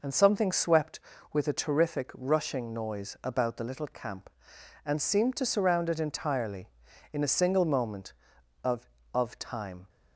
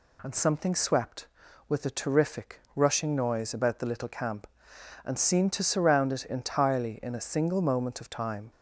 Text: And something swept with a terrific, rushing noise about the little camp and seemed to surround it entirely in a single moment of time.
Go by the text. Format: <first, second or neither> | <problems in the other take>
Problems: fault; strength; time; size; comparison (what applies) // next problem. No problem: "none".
second | says "of" twice; at 9.1 s